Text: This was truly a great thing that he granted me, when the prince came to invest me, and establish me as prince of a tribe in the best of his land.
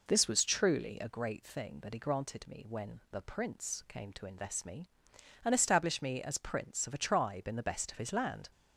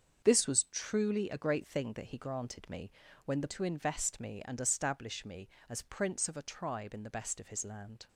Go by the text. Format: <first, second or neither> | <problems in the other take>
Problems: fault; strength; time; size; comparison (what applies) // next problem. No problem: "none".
first | starts louder than the rest; until 1.2 s; 7 dB // skips "prince came"; at 3.4 s